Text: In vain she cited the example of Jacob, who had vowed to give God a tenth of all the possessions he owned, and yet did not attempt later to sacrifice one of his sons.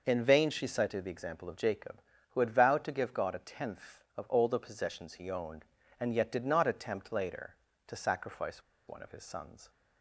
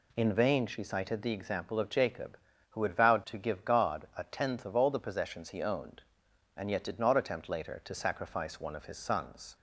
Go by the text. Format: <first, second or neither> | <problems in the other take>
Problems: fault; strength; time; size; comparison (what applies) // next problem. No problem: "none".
second | pauses between "sacrifice" and "one"; slight; at 8.6 s; 0.25 s long